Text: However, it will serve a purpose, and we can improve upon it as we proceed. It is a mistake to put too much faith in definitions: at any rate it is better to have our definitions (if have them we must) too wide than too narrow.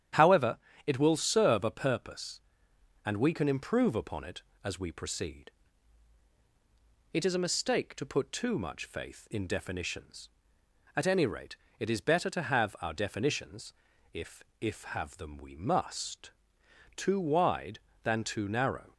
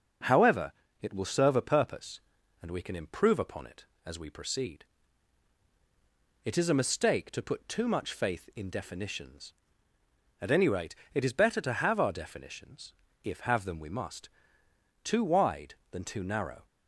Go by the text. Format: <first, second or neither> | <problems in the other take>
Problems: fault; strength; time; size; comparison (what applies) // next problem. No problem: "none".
second | starts louder than the rest; strong; until 1.4 s; 10 dB; noticeable in the second // pauses between "rate" and "it"; slight; at 11.5 s; 0.23 s long; slight in the second // says "if" twice; at 14.6 s